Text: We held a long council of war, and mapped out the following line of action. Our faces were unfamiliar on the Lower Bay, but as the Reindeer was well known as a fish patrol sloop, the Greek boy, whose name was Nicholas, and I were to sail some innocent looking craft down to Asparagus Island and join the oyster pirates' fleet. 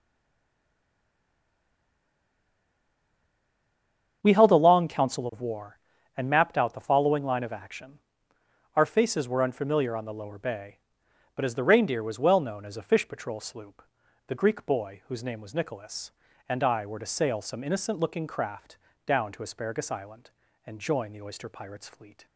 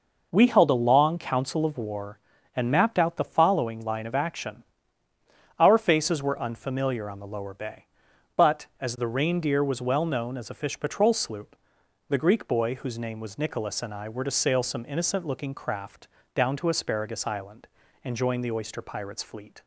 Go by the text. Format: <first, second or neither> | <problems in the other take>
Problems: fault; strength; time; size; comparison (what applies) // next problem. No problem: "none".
second | stays silent before the first word; strong; until 4.2 s; 4.2 s long // starts louder than the rest; strong; until 5.2 s; 7.5 dB // pauses between "craft" and "down"; slight; at 18.7 s; 0.28 s long; slight in the second